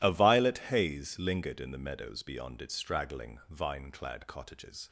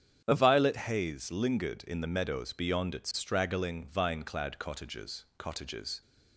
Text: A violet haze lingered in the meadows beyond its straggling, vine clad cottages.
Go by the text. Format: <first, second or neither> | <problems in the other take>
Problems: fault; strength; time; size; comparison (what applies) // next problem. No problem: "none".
first | starts louder than the rest; strong; until 1.2 s; 8 dB // says "cottages" twice; at 5.3 s